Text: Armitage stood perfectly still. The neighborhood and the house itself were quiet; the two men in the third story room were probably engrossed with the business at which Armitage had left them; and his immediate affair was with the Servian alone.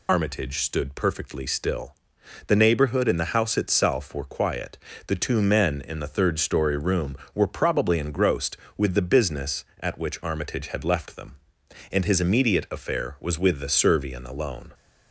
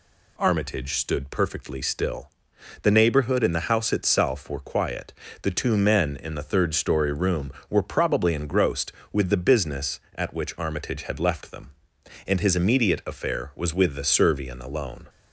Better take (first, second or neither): second